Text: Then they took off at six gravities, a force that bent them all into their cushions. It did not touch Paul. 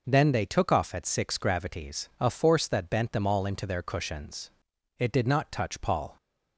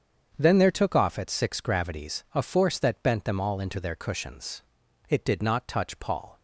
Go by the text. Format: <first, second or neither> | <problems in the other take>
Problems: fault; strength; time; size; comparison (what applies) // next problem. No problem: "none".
first | starts louder than the rest; strong; until 1.3 s; 7.5 dB // says "there" for "they"; at 0.5 s